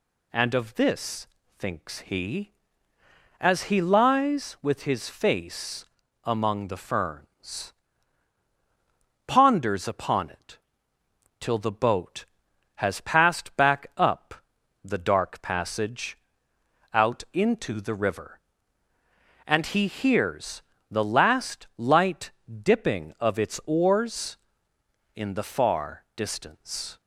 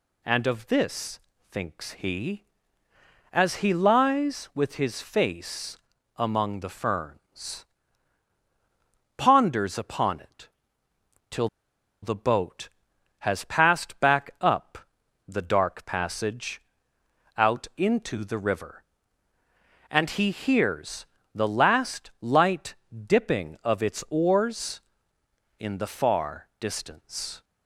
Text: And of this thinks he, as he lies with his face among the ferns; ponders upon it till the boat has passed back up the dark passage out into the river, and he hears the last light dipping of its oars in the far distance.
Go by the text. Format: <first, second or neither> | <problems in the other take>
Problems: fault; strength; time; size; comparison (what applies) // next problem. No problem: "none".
first | pauses between "this" and "thinks"; slight; at 1.1 s; 0.32 s long; slight in the first // pauses between "face" and "among"; at 5.7 s; 0.38 s long; also in the first // pauses between "it" and "till"; noticeable; at 10.4 s; 0.82 s long; noticeable in the first // pauses between "till" and "the"; noticeable; at 11.4 s; 0.54 s long // pauses between "up" and "the"; noticeable; at 14.7 s; 0.48 s long; noticeable in the first // pauses between "passage" and "out"; noticeable; at 16.5 s; 0.78 s long; noticeable in the first // pauses between "hears" and "the"; slight; at 21.0 s; 0.28 s long; slight in the first // pauses between "light" and "dipping"; slight; at 22.7 s; 0.32 s long; slight in the first